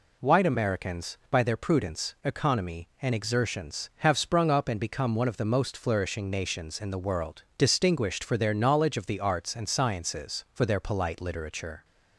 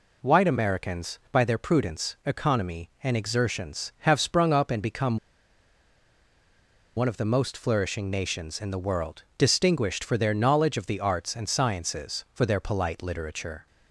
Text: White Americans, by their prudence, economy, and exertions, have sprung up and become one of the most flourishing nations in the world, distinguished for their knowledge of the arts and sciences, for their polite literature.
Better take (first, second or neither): first